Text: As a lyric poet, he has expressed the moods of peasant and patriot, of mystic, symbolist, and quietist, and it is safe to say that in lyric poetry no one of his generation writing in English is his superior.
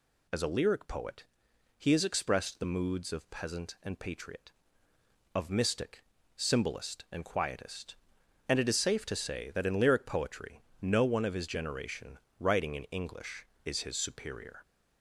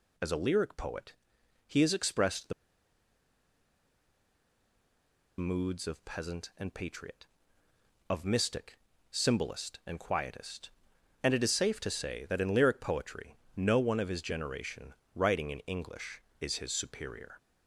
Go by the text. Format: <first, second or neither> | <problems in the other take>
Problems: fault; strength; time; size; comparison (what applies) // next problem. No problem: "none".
first | pauses between "the" and "moods"; strong; at 2.5 s; 2.8 s long // pauses between "poetry" and "no"; slight; at 13.3 s; 0.18 s long; slight in the first // pauses between "generation" and "writing"; slight; at 14.9 s; 0.22 s long; slight in the first